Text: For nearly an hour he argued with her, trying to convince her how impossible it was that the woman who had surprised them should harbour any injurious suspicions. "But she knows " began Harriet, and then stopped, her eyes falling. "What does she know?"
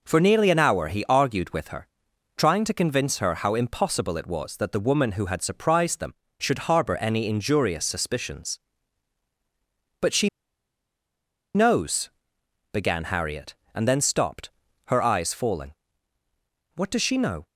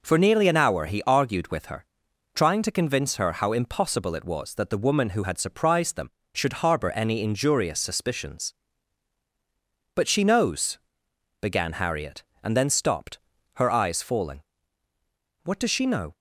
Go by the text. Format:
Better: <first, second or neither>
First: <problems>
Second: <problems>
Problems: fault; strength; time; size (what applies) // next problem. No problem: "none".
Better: second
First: pauses between "she" and "knows"; strong; at 10.2 s; 1.2 s long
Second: none